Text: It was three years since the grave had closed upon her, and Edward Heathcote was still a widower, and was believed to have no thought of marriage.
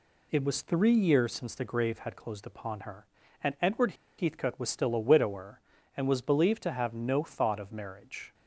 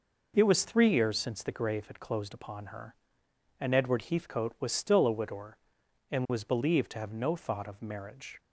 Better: second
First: pauses between "Edward" and "Heathcote"; slight; at 3.9 s; 0.24 s long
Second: none

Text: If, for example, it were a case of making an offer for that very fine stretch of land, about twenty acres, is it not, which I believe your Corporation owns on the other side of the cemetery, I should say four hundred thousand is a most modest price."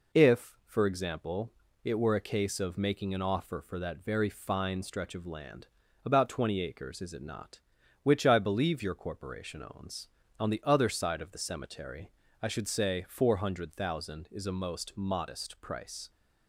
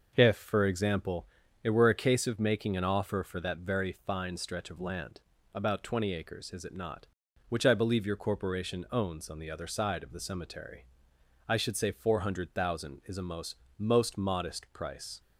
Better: first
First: none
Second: starts louder than the rest; noticeable; until 1.1 s; 6 dB // says "most" twice; at 13.7 s

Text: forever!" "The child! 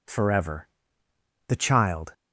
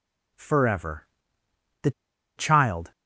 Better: first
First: none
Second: pauses between "The" and "child"; at 1.9 s; 0.45 s long

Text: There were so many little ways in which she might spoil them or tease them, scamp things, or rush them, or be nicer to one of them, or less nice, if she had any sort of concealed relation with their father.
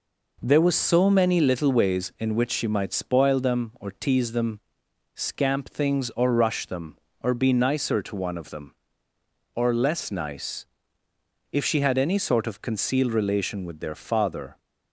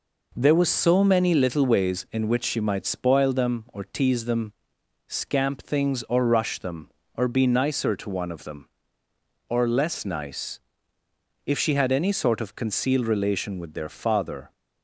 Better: neither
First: none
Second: none

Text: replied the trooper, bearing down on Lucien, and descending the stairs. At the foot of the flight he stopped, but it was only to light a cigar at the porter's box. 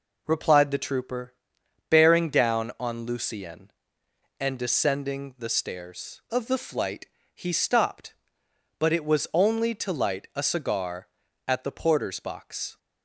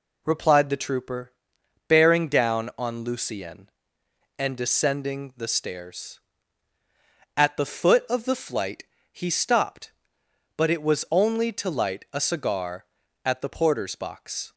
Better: second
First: skips "At the foot"; at 6.2 s // pauses between "flight" and "he"; slight; at 7.0 s; 0.28 s long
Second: pauses between "flight" and "he"; slight; at 8.8 s; 0.28 s long

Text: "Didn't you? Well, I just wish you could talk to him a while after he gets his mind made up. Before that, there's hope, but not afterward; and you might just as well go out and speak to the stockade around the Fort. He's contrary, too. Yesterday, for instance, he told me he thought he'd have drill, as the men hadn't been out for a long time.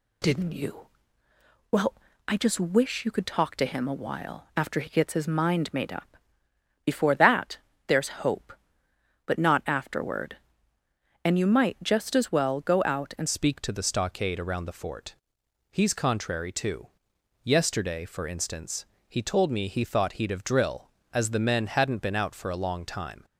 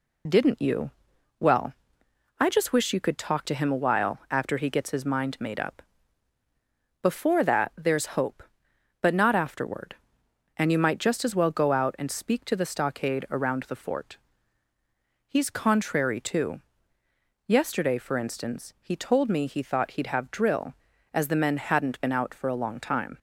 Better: second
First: changes voice at "speak"; from 13.2 s on; 10.0 s long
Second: none

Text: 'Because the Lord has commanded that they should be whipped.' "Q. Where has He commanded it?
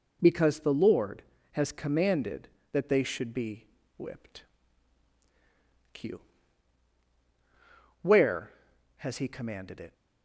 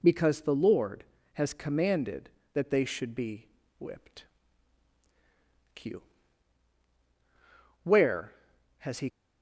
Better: first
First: pauses between "be" and "whipped"; slight; at 3.6 s; 0.30 s long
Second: pauses between "be" and "whipped"; slight; at 3.4 s; 0.30 s long // stops before "commanded it"; at 9.0 s

